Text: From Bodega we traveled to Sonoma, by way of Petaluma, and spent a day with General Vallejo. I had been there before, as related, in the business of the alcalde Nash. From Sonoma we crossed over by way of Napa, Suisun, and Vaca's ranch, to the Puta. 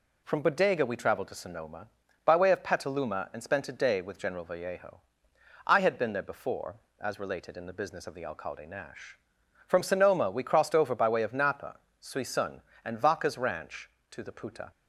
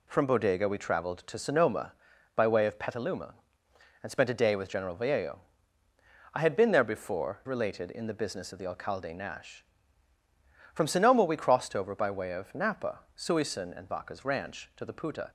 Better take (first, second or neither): first